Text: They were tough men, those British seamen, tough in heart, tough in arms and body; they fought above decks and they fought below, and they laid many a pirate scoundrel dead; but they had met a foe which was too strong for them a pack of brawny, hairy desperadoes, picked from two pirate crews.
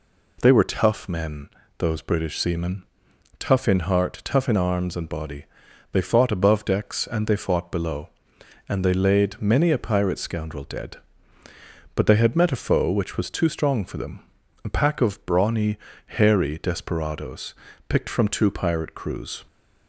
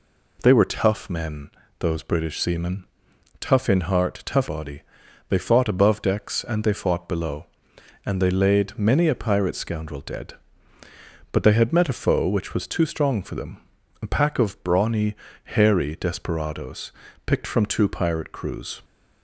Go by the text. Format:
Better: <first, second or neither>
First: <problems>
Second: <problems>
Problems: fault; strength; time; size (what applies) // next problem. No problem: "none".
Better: first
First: pauses between "them" and "a"; at 14.2 s; 0.42 s long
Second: skips "in arms and"; at 4.4 s // pauses between "them" and "a"; at 13.5 s; 0.42 s long